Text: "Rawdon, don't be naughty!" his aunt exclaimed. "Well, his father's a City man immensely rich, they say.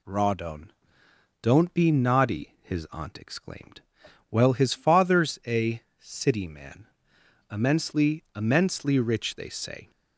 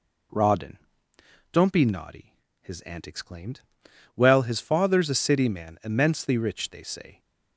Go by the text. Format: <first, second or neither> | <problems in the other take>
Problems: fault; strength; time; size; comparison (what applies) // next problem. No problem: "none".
second | pauses between "a" and "City"; slight; at 5.8 s; 0.20 s long // pauses between "man" and "immensely"; noticeable; at 6.8 s; 0.64 s long // says "immensely" twice; at 8.3 s